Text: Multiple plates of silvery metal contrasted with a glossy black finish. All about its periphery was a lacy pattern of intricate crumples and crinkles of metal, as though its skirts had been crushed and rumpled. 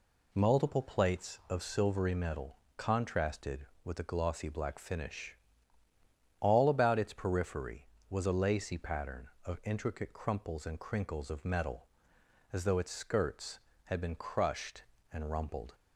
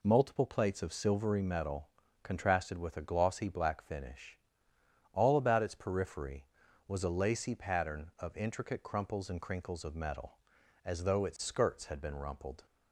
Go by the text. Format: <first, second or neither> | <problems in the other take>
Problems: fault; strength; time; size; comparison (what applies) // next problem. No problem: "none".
first | pauses between "metal" and "contrasted"; slight; at 1.8 s; 0.34 s long; slight in the first // skips "crushed and"; at 12.1 s